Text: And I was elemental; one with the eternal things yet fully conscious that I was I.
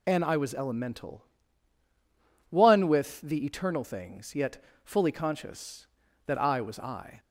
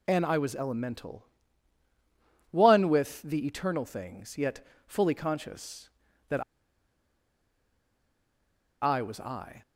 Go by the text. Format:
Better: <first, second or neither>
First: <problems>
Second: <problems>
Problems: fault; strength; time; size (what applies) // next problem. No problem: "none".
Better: first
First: pauses between "yet" and "fully"; slight; at 4.5 s; 0.26 s long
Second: pauses between "yet" and "fully"; slight; at 4.5 s; 0.26 s long // pauses between "that" and "I"; strong; at 6.4 s; 2.3 s long